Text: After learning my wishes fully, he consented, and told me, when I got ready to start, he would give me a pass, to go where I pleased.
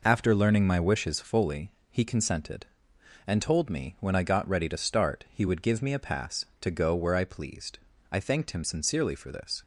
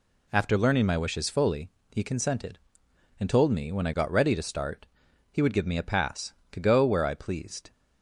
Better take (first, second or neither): second